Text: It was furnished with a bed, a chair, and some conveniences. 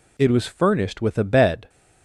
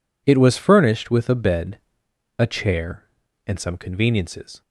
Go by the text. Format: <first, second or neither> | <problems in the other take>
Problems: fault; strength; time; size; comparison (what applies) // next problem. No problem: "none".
second | stops before "a chair and some conveniences"; at 1.6 s